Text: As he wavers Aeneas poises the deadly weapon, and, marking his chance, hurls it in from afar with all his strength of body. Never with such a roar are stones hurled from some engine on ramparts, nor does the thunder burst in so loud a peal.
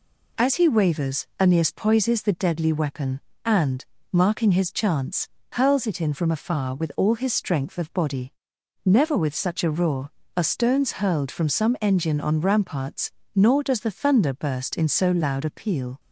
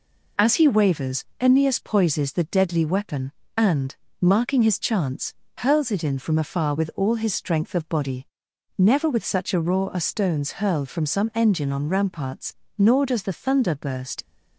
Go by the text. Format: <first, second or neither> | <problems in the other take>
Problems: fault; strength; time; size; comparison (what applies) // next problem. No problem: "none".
first | pauses between "wavers" and "Aeneas"; slight; at 1.2 s; 0.16 s long // stops before "in so loud a peal"; at 14.2 s